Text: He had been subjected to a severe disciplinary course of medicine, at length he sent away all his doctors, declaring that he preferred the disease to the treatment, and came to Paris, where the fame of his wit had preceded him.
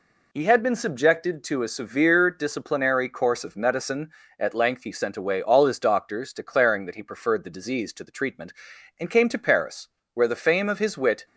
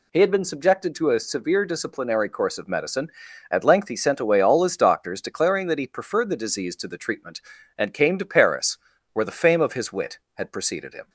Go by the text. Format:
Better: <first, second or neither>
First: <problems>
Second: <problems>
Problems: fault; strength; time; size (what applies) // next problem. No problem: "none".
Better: second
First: stops before "had preceded him"; at 11.2 s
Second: none